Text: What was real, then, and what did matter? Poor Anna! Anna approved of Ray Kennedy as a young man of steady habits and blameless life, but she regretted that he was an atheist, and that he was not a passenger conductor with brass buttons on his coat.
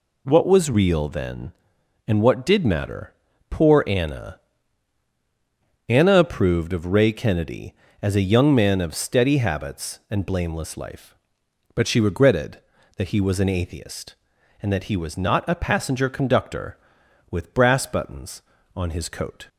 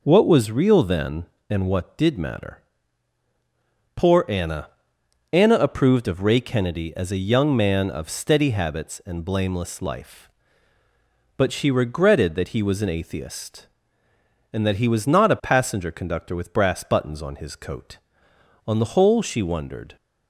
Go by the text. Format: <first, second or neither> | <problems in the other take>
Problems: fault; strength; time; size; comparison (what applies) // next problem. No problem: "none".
first | goes on to say "On the whole she wondered"; noticeable; from 18.6 s on; 1.2 s long